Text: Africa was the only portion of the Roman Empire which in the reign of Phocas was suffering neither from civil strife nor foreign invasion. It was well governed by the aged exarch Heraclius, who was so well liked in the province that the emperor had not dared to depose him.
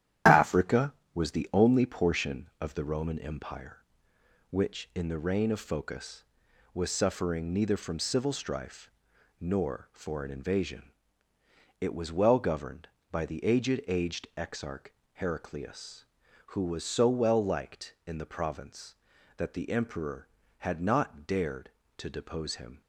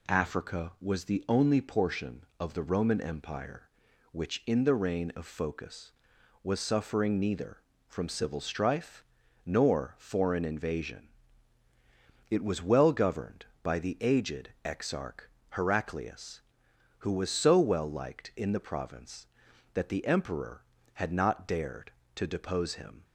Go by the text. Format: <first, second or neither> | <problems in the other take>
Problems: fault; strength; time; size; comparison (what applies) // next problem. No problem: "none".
second | starts louder than the rest; strong; until 1.4 s; 11 dB // pauses between "strife" and "nor"; noticeable; at 8.9 s; 0.48 s long; also in the second // says "aged" twice; at 13.8 s // pauses between "exarch" and "Heraclius"; slight; at 14.9 s; 0.24 s long; slight in the second